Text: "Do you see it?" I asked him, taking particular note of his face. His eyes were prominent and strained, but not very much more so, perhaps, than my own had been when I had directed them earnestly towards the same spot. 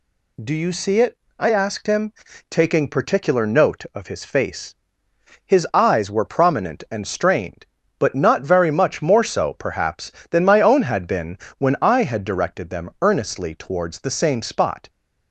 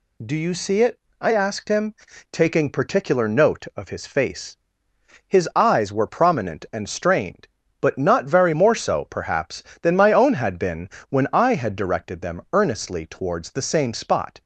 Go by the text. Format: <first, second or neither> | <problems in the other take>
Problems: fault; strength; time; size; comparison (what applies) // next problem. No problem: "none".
first | skips "much"; at 8.5 s // pauses between "been" and "when"; slight; at 10.8 s; 0.22 s long; slight in the first